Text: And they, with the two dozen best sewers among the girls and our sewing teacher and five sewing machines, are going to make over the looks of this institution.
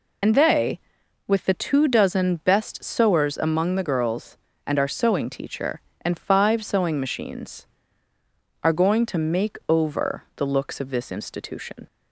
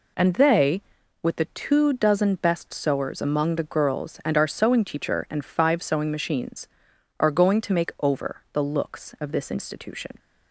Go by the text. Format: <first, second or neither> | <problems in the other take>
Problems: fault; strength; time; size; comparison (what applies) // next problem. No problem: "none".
second | loses the start of "And"; at 0.2 s; 65 ms